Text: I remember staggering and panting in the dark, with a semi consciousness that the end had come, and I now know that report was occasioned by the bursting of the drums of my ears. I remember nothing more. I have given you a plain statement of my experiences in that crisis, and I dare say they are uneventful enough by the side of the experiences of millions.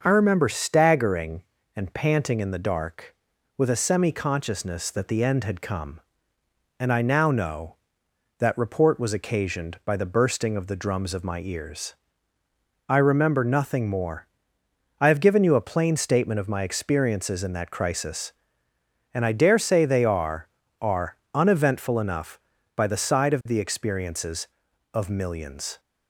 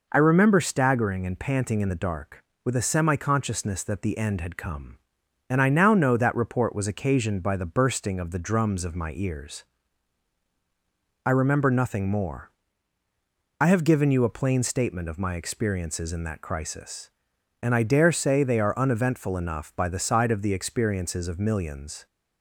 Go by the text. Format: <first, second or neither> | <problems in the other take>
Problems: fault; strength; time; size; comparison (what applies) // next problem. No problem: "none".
second | starts louder than the rest; noticeable; until 1.0 s; 6 dB // says "are" twice; at 20.7 s